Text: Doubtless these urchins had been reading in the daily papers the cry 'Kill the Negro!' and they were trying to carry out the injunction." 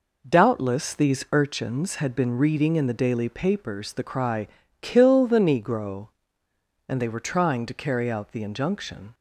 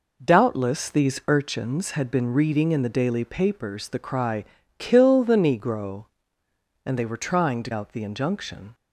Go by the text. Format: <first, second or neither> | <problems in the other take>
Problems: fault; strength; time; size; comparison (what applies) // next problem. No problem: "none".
first | pauses between "cry" and "Kill"; slight; at 4.4 s; 0.34 s long; slight in the first // skips "carry"; at 7.7 s